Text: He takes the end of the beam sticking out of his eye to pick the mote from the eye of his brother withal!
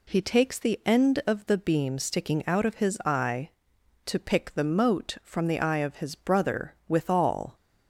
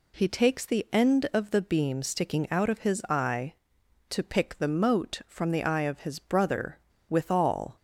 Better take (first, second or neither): first